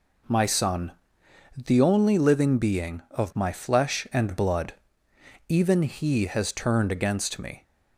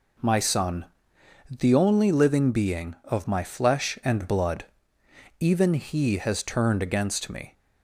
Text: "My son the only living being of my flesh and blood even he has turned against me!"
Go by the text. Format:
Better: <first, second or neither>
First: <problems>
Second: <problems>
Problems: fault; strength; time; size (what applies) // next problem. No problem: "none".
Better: neither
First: pauses between "son" and "the"; noticeable; at 0.9 s; 0.62 s long // pauses between "blood" and "even"; noticeable; at 4.7 s; 0.72 s long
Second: pauses between "son" and "the"; noticeable; at 0.8 s; 0.62 s long // pauses between "blood" and "even"; noticeable; at 4.6 s; 0.72 s long